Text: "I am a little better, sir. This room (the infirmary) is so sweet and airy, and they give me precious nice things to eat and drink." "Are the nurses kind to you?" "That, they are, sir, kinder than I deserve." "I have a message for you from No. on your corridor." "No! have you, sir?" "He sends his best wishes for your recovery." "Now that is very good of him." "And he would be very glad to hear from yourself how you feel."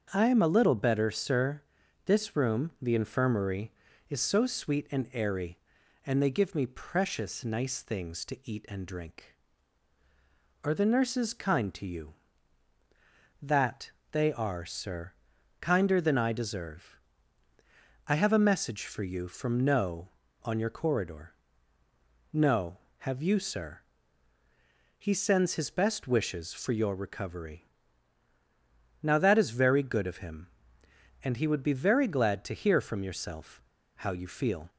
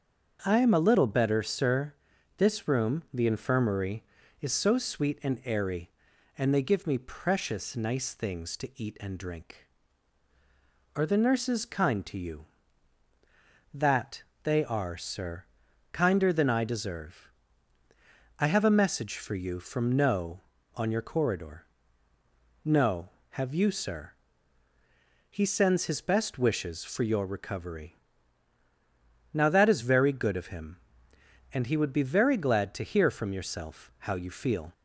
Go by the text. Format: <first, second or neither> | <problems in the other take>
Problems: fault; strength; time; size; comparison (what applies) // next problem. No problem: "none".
second | starts louder than the rest; until 1.1 s; 6.5 dB; also in the second // pauses between "yourself" and "how"; slight; at 33.6 s; 0.32 s long